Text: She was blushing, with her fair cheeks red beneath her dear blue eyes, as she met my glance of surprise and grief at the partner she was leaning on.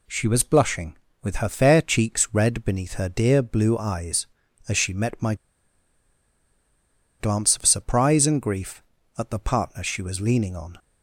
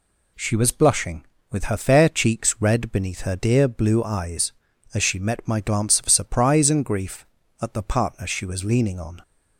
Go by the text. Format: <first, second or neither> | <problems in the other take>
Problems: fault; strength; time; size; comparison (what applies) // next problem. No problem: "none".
second | pauses between "my" and "glance"; strong; at 5.3 s; 1.8 s long